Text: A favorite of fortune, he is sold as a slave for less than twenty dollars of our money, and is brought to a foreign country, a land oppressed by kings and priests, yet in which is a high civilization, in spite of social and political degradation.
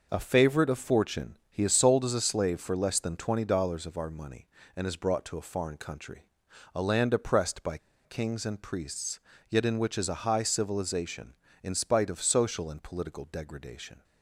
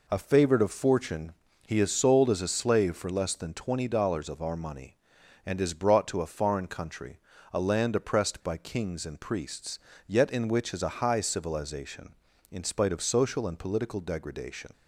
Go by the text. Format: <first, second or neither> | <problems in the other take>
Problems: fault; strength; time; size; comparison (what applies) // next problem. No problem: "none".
second | pauses between "by" and "kings"; slight; at 7.7 s; 0.27 s long